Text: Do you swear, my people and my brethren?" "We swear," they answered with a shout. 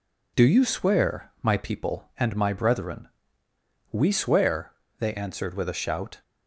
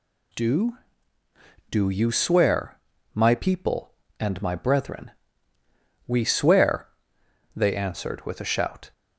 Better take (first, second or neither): first